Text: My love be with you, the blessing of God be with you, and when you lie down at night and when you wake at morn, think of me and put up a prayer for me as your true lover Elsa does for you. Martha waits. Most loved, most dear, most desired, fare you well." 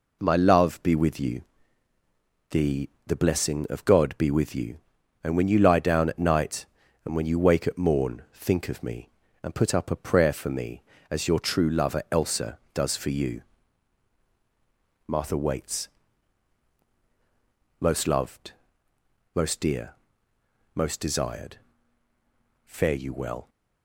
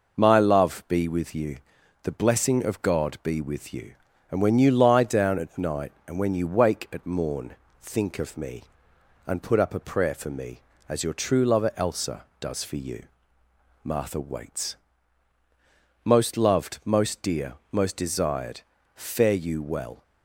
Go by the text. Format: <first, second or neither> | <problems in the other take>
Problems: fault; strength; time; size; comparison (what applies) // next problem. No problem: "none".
second | says "the" twice; at 3.0 s